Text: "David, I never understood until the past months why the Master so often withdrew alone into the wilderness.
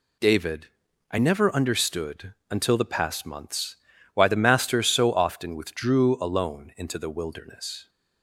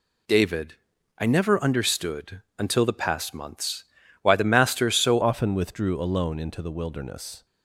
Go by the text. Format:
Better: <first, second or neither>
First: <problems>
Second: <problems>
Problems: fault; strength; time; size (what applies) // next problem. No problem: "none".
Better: first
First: pauses between "understood" and "until"; slight; at 2.3 s; 0.16 s long // pauses between "months" and "why"; at 3.7 s; 0.38 s long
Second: pauses between "understood" and "until"; slight; at 2.4 s; 0.16 s long // pauses between "months" and "why"; at 3.8 s; 0.38 s long // changes voice at "often"; from 5.2 s on; 2.2 s long